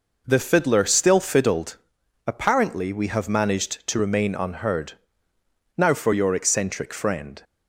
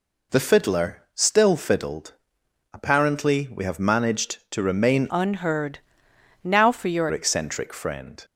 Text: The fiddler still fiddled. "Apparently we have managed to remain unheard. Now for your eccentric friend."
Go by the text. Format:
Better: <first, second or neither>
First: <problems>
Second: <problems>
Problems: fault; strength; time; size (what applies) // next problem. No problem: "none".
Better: first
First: none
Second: changes voice from "unheard" to "your"; from 5.1 to 7.0 s; 1.9 s long